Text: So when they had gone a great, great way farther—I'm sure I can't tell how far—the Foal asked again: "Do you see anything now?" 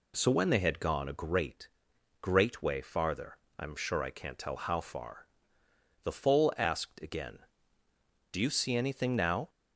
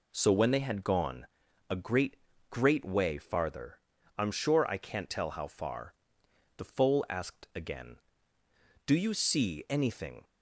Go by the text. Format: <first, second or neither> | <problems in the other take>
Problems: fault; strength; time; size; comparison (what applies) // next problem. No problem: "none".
first | pauses between "gone" and "a"; at 1.2 s; 0.44 s long // stops before "now"; at 10.2 s